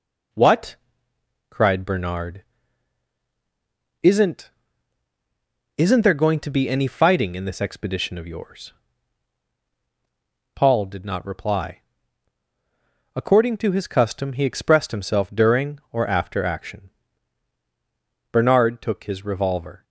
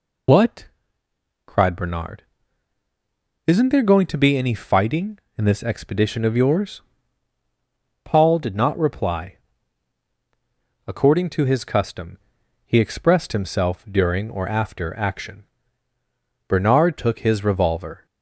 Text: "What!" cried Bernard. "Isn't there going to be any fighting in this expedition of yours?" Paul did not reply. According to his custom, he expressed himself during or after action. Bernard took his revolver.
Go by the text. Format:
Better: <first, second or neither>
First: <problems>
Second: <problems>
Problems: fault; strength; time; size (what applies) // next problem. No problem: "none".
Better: second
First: says "Isn't" twice; at 5.7 s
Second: none